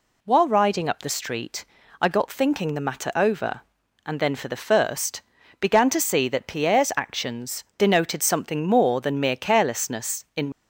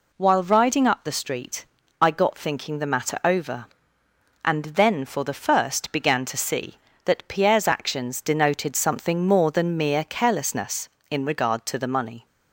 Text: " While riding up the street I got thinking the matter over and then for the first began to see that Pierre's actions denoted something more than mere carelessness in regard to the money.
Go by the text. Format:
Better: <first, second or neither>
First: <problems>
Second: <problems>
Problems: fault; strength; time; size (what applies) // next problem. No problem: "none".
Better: second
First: pauses between "street" and "I"; slight; at 1.6 s; 0.34 s long // pauses between "first" and "began"; at 5.2 s; 0.38 s long // stops before "regard to the money"; at 10.5 s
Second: pauses between "street" and "I"; slight; at 1.6 s; 0.34 s long